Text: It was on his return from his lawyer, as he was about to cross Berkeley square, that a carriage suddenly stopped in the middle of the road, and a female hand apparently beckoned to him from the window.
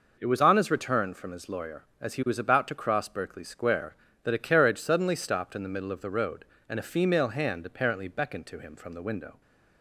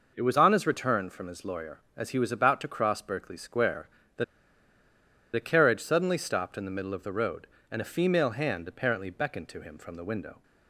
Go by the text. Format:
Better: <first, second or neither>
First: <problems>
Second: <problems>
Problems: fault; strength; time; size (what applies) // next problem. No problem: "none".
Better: first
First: none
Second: pauses between "that" and "a"; at 4.2 s; 1.1 s long